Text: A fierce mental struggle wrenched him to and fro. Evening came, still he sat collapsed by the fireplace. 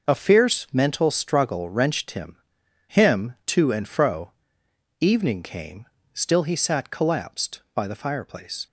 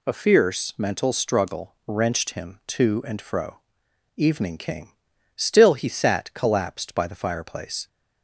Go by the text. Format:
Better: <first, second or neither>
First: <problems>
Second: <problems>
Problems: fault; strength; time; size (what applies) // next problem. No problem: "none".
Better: second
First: says "him" twice; at 2.8 s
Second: none